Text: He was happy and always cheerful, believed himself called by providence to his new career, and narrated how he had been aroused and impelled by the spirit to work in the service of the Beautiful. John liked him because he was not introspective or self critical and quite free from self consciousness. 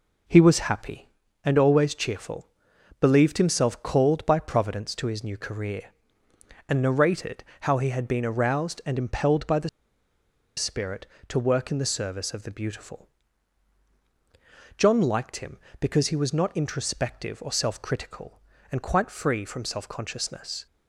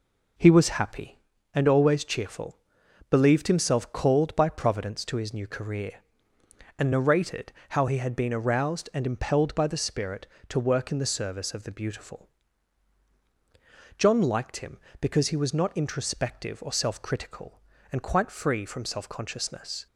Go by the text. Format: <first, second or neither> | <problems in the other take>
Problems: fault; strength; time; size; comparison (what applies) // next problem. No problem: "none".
second | pauses between "narrated" and "how"; slight; at 7.4 s; 0.16 s long; slight in the second // pauses between "the" and "spirit"; noticeable; at 9.6 s; 0.88 s long